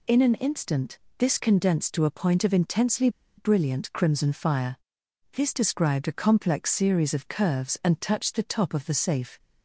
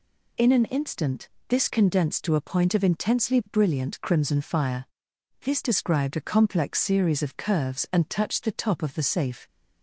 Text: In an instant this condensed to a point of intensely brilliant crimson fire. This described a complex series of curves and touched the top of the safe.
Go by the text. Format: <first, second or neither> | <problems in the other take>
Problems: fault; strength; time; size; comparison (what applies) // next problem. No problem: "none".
second | pauses between "instant" and "this"; slight; at 0.9 s; 0.20 s long; slight in the second // pauses between "intensely" and "brilliant"; slight; at 3.0 s; 0.28 s long